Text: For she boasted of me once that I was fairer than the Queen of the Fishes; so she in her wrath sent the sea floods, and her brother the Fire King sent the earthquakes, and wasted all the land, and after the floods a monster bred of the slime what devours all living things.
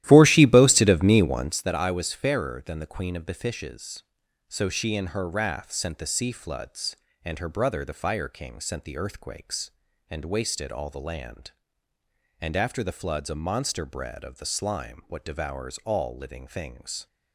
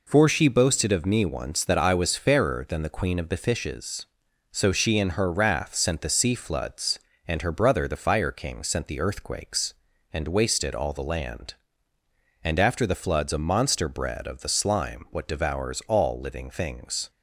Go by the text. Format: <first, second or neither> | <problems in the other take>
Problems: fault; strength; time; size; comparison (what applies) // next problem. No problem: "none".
second | starts louder than the rest; strong; until 1.6 s; 14 dB